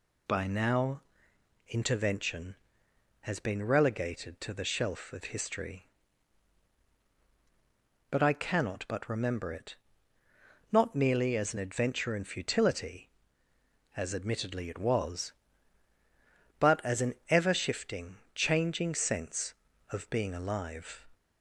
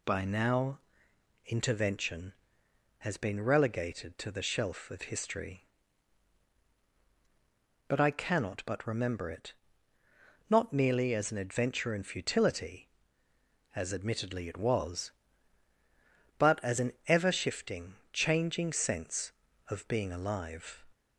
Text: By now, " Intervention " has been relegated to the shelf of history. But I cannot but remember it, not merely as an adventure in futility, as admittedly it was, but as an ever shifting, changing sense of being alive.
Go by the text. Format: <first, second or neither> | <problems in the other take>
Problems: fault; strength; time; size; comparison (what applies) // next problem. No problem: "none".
neither | pauses between "an" and "ever"; slight; the same in both